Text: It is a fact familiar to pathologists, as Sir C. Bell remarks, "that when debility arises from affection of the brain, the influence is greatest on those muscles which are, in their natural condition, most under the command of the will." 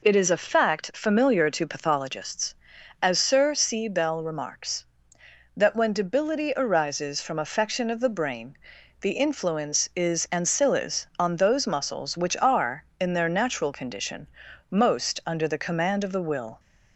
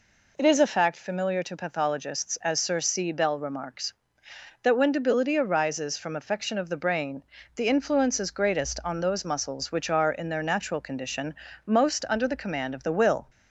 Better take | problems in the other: second | says "ancillis" for "greatest"; at 10.2 s

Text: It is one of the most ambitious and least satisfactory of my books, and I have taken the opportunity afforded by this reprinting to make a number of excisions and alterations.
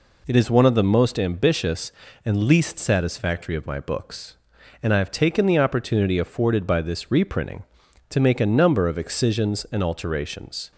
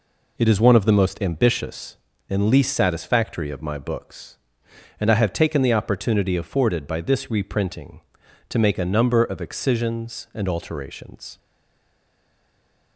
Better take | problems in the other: first | stays silent after the last word; noticeable; from 11.3 s on; 1.6 s long

